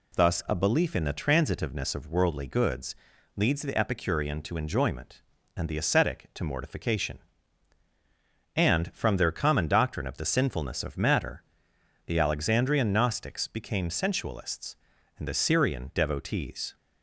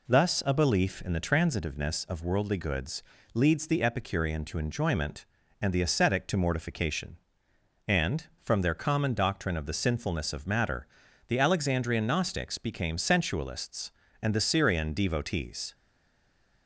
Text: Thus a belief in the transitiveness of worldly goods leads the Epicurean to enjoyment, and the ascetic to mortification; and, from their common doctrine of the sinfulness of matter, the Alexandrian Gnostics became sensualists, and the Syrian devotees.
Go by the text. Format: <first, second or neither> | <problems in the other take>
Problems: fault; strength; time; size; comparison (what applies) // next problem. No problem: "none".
first | pauses between "goods" and "leads"; slight; at 3.0 s; 0.32 s long; also in the first // stays silent after the last word; slight; from 15.7 s on; 0.9 s long